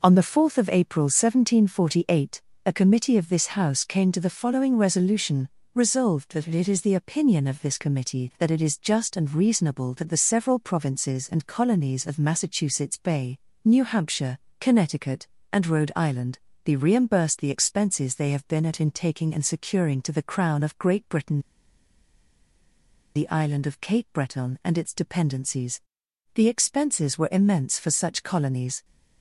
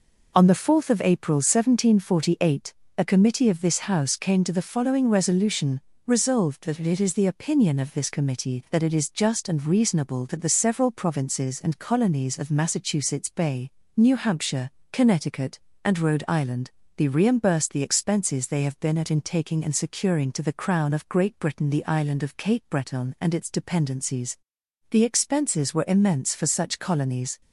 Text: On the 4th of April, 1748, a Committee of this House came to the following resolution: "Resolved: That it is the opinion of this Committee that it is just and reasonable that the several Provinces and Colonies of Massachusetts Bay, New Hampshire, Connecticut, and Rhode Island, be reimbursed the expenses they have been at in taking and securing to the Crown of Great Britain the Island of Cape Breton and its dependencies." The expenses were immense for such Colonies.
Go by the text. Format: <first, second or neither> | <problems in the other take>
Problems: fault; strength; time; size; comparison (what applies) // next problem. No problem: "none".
second | pauses between "Britain" and "the"; strong; at 21.4 s; 1.7 s long